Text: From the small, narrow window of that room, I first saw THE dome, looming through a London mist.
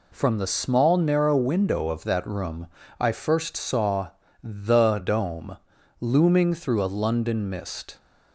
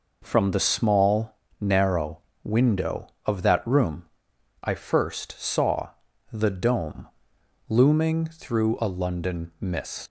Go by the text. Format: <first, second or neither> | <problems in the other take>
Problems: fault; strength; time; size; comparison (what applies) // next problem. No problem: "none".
first | pauses between "narrow" and "window"; slight; at 2.2 s; 0.24 s long // pauses between "saw" and "THE"; at 5.8 s; 0.42 s long; slight in the first // leaves "mist" unfinished; at 10.0 s; 135 ms